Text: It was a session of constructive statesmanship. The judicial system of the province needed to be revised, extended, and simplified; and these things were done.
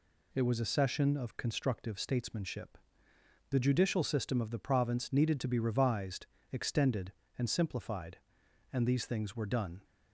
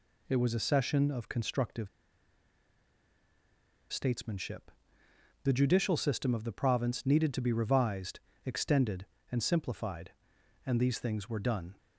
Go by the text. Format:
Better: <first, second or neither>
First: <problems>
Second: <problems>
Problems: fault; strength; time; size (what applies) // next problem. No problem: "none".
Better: first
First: none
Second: pauses between "constructive" and "statesmanship"; strong; at 1.8 s; 2.0 s long